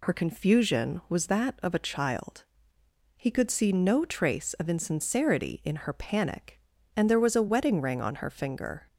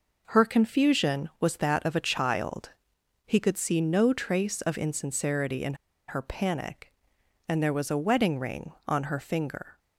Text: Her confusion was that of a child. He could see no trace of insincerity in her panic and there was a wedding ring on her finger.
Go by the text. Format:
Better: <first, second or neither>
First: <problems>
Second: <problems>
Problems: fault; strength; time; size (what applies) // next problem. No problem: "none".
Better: first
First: none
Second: pauses between "in" and "her"; slight; at 5.7 s; 0.33 s long